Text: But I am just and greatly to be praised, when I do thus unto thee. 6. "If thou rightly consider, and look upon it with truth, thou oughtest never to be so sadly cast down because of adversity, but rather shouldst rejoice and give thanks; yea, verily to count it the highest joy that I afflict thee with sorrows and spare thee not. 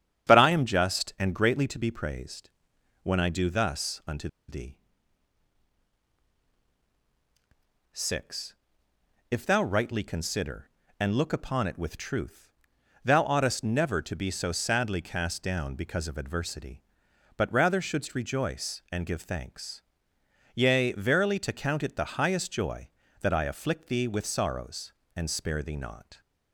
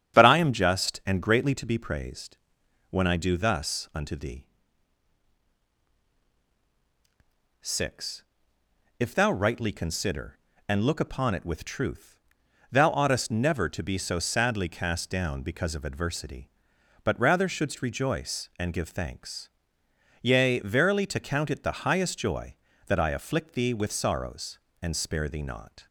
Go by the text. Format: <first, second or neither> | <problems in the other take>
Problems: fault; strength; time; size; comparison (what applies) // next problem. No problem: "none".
second | starts louder than the rest; strong; until 1.3 s; 8.5 dB; strong in the second // pauses between "unto" and "thee"; slight; at 4.2 s; 0.20 s long